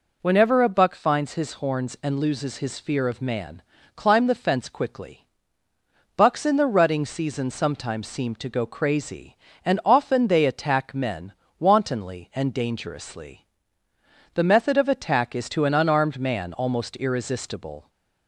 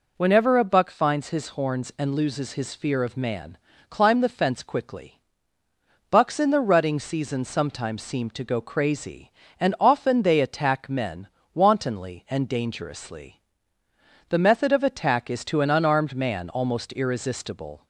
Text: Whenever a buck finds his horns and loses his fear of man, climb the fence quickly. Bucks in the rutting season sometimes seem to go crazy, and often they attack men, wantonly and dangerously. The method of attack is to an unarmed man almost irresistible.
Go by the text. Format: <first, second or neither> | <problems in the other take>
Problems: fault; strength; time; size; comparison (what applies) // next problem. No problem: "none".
neither | none